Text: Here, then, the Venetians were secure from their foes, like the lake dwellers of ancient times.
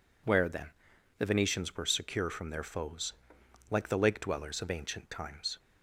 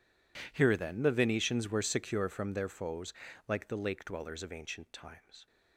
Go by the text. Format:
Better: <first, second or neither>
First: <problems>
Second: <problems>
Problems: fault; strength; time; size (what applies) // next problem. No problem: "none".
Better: second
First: says "Where" for "Here"; at 0.2 s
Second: none